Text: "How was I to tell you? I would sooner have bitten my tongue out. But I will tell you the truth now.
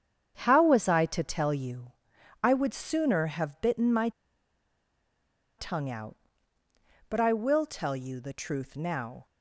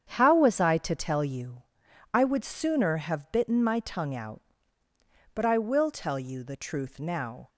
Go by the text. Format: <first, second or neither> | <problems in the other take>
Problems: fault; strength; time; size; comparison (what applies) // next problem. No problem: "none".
second | starts louder than the rest; strong; until 1.4 s; 8 dB; strong in the second // pauses between "my" and "tongue"; strong; at 4.0 s; 1.4 s long